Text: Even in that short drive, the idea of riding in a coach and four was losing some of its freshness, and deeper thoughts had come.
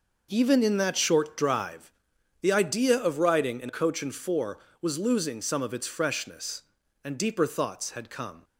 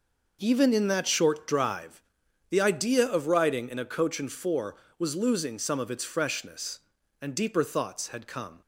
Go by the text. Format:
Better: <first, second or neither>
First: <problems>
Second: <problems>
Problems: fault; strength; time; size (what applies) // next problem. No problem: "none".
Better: second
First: skips "a"; at 3.6 s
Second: none